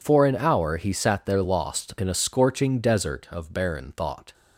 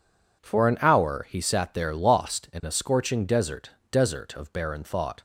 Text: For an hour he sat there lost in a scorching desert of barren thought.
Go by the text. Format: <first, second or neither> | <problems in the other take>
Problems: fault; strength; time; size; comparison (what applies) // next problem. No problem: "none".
first | says "desert" twice; at 3.9 s